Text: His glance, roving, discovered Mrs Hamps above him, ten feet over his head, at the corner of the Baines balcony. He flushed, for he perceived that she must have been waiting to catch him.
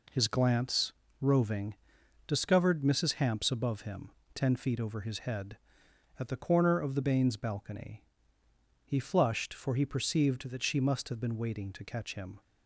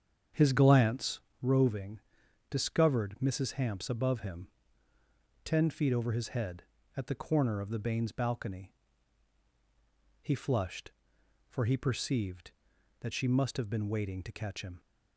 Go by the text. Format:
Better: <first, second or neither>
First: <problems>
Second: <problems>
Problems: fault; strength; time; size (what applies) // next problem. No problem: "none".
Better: first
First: none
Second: starts louder than the rest; strong; until 1.3 s; 8 dB